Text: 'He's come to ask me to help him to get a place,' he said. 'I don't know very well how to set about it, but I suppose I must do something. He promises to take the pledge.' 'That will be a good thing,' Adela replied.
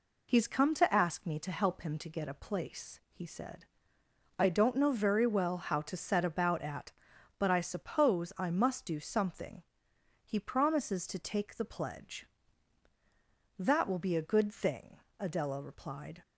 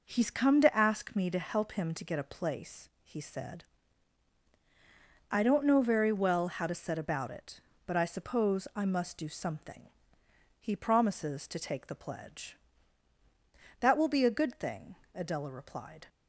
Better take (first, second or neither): second